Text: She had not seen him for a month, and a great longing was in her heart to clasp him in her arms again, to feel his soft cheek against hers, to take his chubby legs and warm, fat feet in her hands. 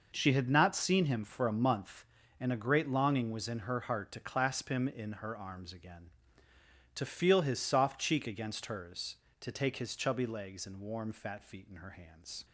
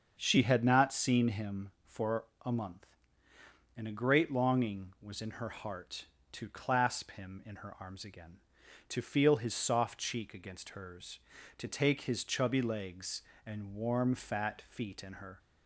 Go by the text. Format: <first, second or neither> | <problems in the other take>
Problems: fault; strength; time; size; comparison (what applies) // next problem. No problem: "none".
first | starts louder than the rest; until 1.2 s; 7 dB // pauses between "for" and "a"; slight; at 2.2 s; 0.20 s long // stops before "hands"; at 15.3 s